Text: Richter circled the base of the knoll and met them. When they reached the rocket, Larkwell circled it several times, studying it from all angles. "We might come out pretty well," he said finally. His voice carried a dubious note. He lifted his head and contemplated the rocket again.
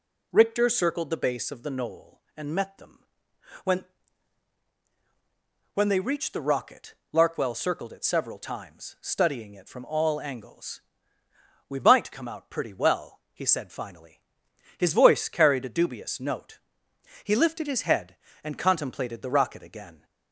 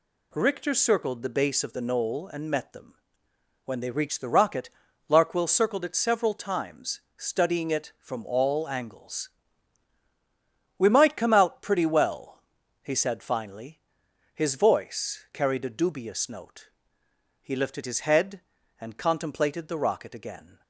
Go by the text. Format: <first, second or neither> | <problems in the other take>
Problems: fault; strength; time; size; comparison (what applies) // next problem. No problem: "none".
second | says "When" twice; at 5.7 s